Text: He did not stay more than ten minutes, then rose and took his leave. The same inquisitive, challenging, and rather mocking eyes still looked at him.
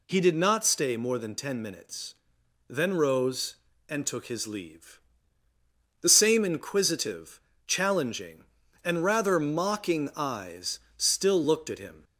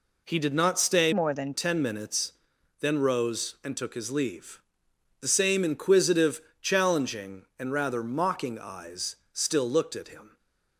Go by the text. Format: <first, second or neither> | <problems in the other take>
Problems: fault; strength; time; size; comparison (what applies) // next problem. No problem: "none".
first | changes voice from "more" to "than"; from 1.1 to 1.5 s; 0.4 s long // pauses between "eyes" and "still"; slight; at 9.1 s; 0.18 s long; slight in the first // stays silent after the last word; slight; from 10.2 s on; 0.5 s long